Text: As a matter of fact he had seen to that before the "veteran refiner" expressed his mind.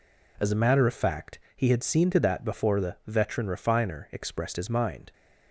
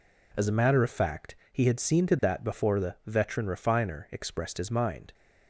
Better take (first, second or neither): neither